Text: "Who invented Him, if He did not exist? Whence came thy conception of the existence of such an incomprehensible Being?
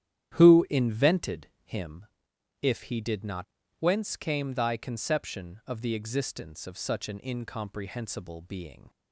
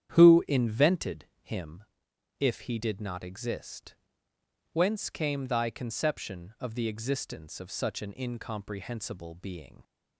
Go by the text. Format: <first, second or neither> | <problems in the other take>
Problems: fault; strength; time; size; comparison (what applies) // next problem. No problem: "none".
second | starts louder than the rest; strong; until 1.4 s; 11 dB; strong in the second // skips "exist"; at 3.6 s